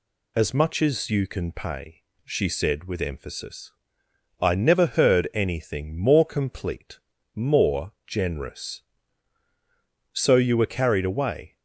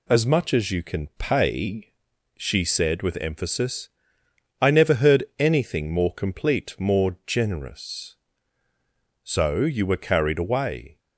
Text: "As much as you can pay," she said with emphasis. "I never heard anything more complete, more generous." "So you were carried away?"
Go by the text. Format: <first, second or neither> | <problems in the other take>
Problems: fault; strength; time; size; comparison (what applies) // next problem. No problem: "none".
neither | none